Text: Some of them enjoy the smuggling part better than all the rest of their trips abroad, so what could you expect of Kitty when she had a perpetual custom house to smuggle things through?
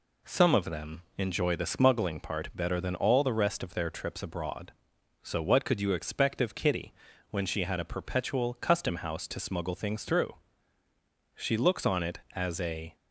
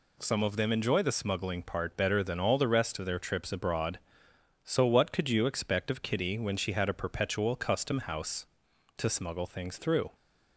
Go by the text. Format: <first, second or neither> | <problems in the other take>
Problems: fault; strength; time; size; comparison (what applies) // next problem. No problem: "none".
second | pauses between "them" and "enjoy"; slight; at 1.0 s; 0.16 s long // pauses between "Kitty" and "when"; at 6.9 s; 0.38 s long // goes on to say "She looks on it as a"; from 11.3 s on; 1.6 s long